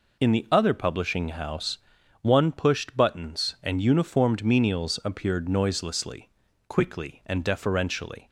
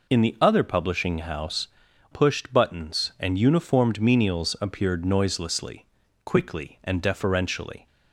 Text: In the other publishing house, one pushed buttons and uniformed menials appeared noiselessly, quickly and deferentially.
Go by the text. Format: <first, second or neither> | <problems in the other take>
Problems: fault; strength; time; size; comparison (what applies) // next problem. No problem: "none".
first | skips "one"; at 1.8 s